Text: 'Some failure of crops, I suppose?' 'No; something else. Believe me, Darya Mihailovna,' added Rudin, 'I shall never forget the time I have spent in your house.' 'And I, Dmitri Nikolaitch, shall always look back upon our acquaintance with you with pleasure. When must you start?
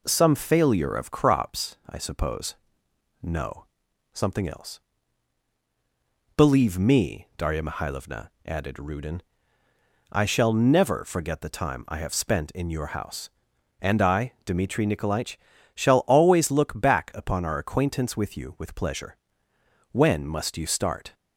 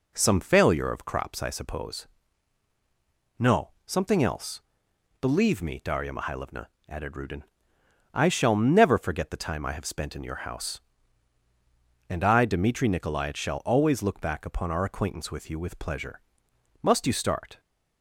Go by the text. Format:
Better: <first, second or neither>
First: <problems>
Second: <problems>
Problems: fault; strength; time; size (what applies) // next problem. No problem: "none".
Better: first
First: none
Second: skips "When"; at 16.5 s